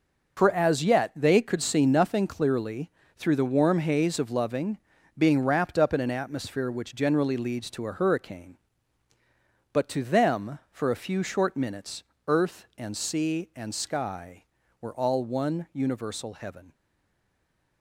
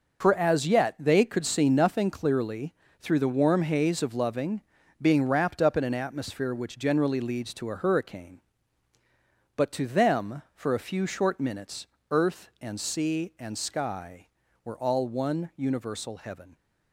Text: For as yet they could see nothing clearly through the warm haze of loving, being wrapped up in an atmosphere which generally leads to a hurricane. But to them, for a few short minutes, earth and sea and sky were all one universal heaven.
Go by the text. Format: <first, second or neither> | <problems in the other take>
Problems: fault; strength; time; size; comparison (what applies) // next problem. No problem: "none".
second | pauses between "clearly" and "through"; slight; at 2.9 s; 0.24 s long; slight in the second // stays silent after the last word; from 16.7 s on; 1.1 s long